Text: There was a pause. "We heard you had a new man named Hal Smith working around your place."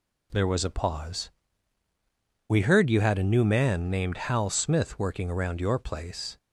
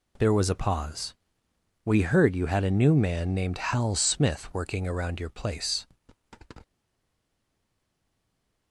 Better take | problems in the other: first | stays silent after the last word; noticeable; from 6.6 s on; 2.1 s long

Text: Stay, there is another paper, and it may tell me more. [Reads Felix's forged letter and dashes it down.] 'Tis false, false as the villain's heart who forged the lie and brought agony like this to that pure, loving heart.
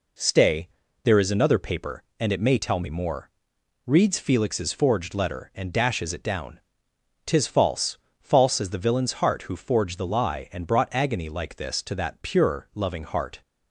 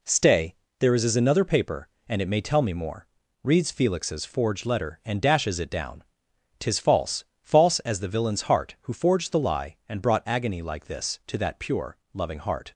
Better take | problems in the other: first | says "is" twice; at 1.0 s

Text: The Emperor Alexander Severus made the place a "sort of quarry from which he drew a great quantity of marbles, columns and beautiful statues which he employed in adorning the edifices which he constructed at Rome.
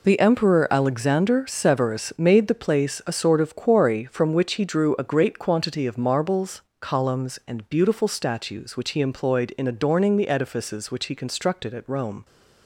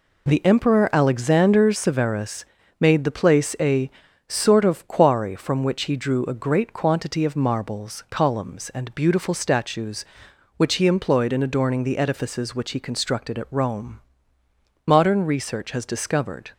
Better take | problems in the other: first | pauses between "Severus" and "made"; at 2.4 s; 0.38 s long // pauses between "a" and "sort"; at 3.8 s; 0.38 s long // goes on to say "Modern research has discovered"; from 14.8 s on; 1.6 s long

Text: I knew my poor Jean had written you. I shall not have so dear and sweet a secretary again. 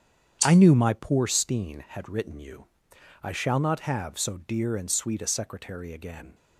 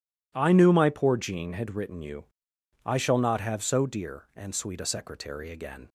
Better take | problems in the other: second | starts louder than the rest; strong; until 1.4 s; 8.5 dB // says "Steen" for "Jean"; at 1.2 s

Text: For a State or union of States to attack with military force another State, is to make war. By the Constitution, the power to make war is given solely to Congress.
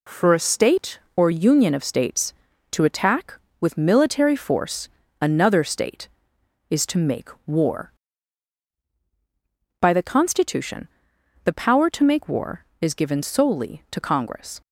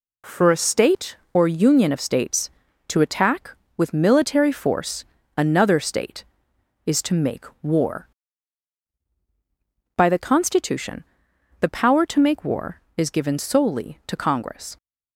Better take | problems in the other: neither | pauses between "force" and "another"; slight; the same in both // pauses between "make" and "war"; slight; the same in both

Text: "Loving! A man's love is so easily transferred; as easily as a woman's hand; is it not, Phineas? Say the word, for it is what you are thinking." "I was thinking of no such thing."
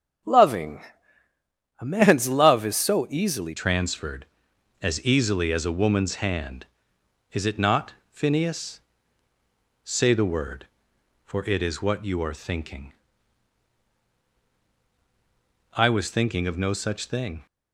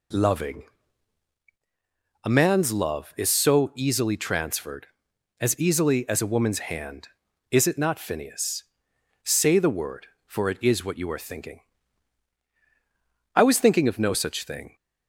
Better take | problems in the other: second | starts louder than the rest; strong; until 2.2 s; 7.5 dB // changes voice at "transferred"; from 3.5 s on; 13.9 s long

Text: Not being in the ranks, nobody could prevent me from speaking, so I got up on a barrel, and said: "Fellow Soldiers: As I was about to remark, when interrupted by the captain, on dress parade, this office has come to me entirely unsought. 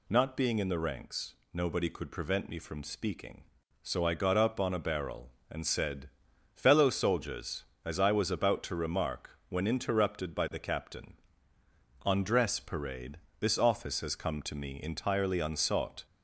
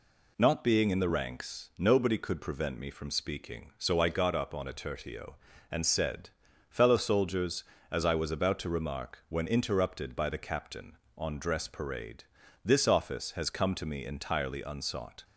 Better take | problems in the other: first | says "tertio" for "barrel"; at 4.7 s

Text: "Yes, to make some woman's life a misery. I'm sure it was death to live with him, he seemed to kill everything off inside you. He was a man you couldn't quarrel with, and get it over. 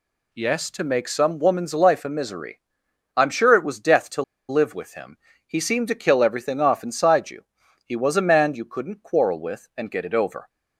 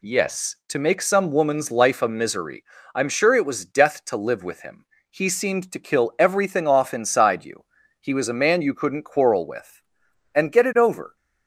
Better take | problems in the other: second | pauses between "to" and "live"; slight; at 4.2 s; 0.27 s long

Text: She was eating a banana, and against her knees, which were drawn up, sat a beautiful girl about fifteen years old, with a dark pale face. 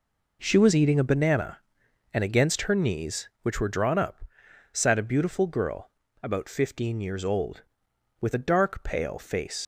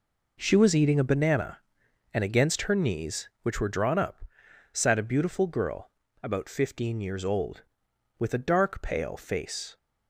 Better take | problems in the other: second | pauses between "girl" and "about"; slight; at 5.9 s; 0.32 s long; slight in the second // leaves "face" unfinished; at 9.6 s; 135 ms

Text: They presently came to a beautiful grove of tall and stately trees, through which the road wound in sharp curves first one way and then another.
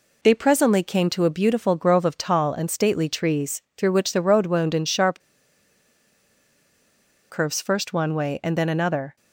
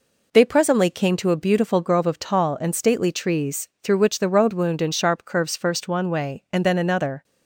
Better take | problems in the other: second | pauses between "sharp" and "curves"; strong; at 5.2 s; 2.0 s long

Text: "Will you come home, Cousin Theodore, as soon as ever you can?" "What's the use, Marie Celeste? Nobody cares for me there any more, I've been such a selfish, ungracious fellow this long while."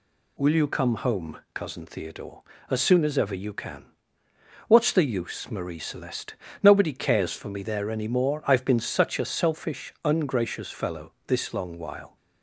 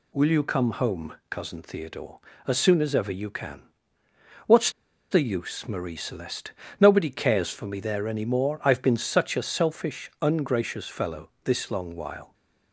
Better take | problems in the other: first | pauses between "What's" and "the"; at 4.7 s; 0.40 s long

